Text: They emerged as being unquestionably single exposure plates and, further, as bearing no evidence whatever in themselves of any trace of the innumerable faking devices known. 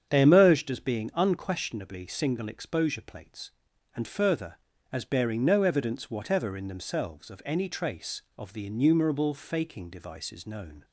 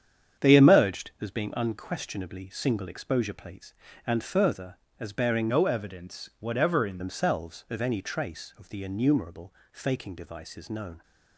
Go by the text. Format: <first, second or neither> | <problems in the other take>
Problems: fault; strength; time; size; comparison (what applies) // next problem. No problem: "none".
first | starts louder than the rest; strong; until 1.5 s; 8 dB; strong in the first // changes voice from "no" to "in"; from 5.4 to 6.9 s; 1.5 s long // pauses between "innumerable" and "faking"; slight; at 9.5 s; 0.18 s long